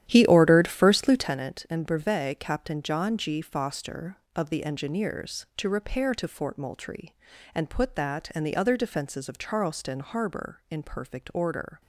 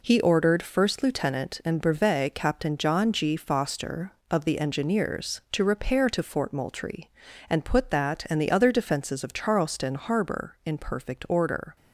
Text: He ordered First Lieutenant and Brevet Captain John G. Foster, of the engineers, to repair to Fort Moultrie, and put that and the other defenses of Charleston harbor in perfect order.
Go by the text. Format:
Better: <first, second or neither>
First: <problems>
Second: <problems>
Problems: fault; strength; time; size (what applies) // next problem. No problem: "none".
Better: second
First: starts louder than the rest; strong; until 1.3 s; 11.5 dB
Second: none